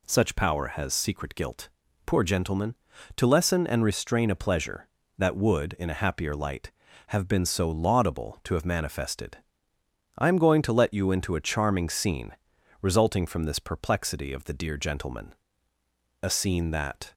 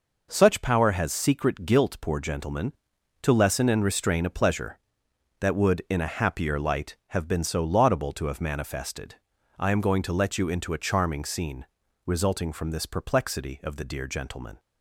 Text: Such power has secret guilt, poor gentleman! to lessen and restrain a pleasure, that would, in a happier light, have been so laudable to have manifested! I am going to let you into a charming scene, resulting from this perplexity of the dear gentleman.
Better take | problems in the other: second | goes on to say "A scene that"; noticeable; from 16.2 s on; 0.92 s long

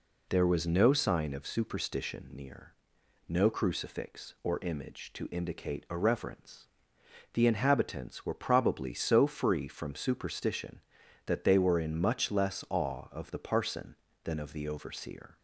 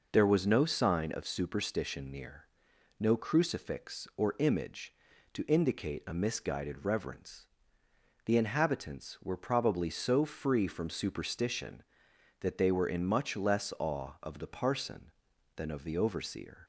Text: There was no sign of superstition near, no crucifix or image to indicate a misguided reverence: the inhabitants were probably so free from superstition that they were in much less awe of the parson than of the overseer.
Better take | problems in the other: second | skips "misguided"; at 5.9 s

